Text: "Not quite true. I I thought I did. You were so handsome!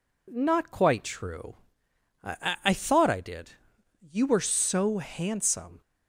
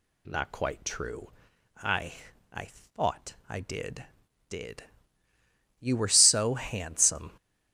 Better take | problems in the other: first | pauses between "I" and "I"; at 2.1 s; 0.40 s long // says "did" twice; at 4.4 s

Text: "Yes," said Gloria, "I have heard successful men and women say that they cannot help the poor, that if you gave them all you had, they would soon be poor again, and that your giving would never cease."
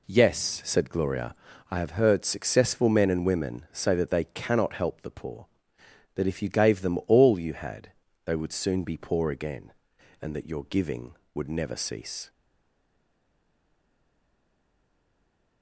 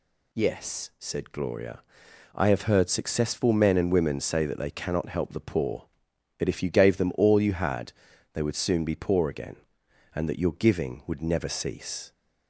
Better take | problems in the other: second | stays silent after the last word; strong; from 12.2 s on; 3.4 s long

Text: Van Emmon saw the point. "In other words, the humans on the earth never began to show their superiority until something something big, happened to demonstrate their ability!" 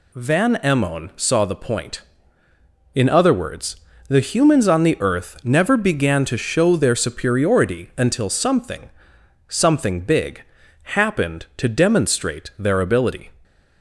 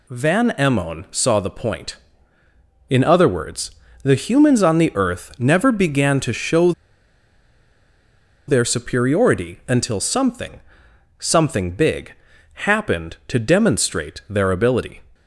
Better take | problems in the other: first | pauses between "show" and "their"; strong; at 6.7 s; 1.7 s long // pauses between "something" and "something"; noticeable; at 10.5 s; 0.62 s long; noticeable in the first

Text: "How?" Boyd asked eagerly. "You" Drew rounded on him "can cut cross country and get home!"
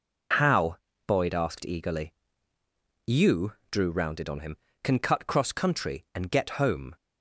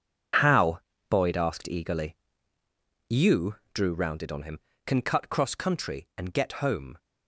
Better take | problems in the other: first | gets quieter; strong; throughout; 11.5 dB // pauses between "You" and "Drew"; slight; at 3.5 s; 0.18 s long; slight in the first

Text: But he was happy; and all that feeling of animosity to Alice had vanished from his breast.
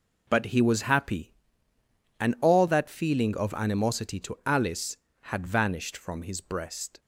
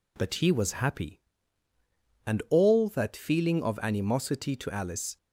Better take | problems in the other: first | stops before "had vanished from his breast"; at 5.1 s

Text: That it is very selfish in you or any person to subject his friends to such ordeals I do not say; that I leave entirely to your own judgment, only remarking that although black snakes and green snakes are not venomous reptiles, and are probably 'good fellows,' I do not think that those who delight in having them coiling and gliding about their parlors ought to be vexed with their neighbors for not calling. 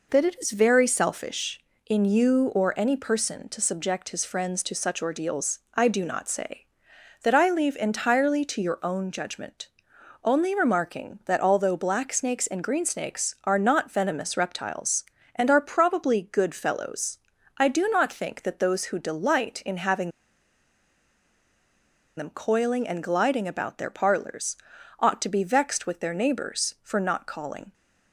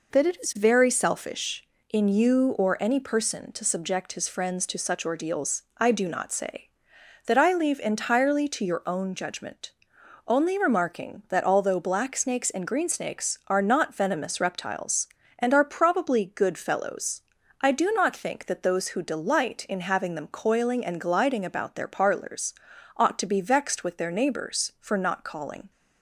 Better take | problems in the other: second | pauses between "ordeals" and "I"; slight; at 5.5 s; 0.16 s long; slight in the second // pauses between "having" and "them"; strong; at 20.1 s; 2.0 s long // pauses between "parlors" and "ought"; noticeable; at 24.5 s; 0.46 s long; noticeable in the second

